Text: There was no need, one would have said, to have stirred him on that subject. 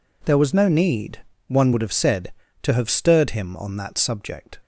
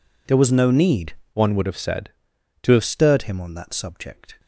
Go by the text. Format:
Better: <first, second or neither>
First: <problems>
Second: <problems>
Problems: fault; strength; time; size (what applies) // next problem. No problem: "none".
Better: first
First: none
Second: changes voice from "one" to "have"; from 1.3 to 2.8 s; 1.5 s long